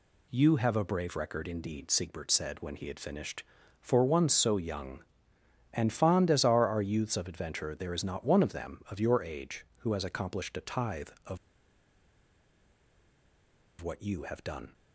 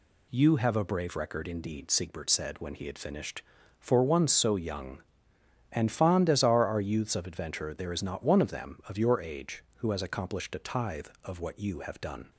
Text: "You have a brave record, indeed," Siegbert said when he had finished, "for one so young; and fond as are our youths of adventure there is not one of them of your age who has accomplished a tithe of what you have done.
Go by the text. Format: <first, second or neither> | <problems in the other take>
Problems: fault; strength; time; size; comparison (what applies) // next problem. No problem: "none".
second | pauses between "of" and "what"; strong; at 11.3 s; 2.4 s long